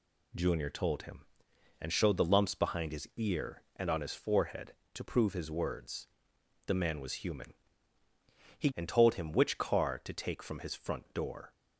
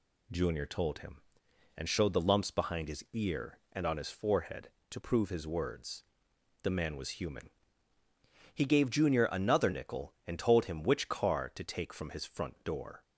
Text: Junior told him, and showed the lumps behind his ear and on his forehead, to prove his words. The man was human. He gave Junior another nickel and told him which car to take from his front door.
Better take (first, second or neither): second